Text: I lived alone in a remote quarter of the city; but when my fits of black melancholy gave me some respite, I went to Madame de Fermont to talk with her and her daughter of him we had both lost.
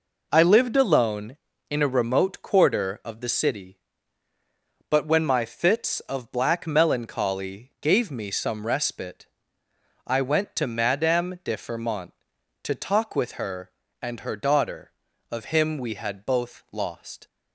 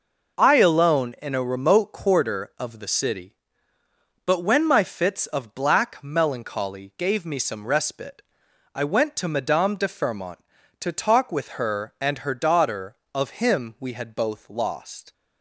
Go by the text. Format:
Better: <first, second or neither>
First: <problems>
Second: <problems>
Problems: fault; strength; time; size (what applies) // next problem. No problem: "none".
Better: first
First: none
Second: skips "lived"; at 0.5 s